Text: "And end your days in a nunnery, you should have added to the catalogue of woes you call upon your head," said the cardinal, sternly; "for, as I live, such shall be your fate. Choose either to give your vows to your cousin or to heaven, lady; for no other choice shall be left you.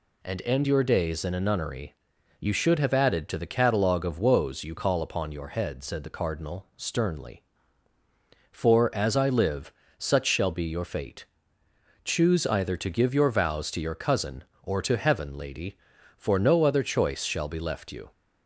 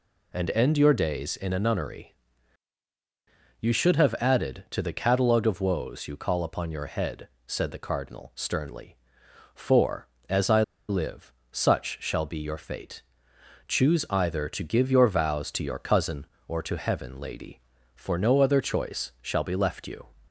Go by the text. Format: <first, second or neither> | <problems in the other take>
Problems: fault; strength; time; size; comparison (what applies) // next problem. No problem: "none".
first | pauses between "I" and "live"; slight; at 10.6 s; 0.26 s long